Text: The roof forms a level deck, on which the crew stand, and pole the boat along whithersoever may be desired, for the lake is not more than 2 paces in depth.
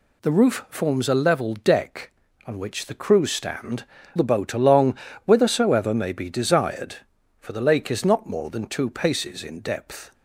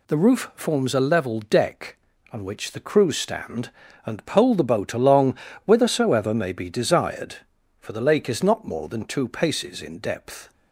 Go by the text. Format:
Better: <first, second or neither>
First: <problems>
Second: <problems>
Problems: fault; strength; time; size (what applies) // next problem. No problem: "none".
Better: second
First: skips "and pole"; at 4.0 s // pauses between "along" and "whithersoever"; slight; at 4.9 s; 0.30 s long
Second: pauses between "along" and "whithersoever"; slight; at 5.3 s; 0.30 s long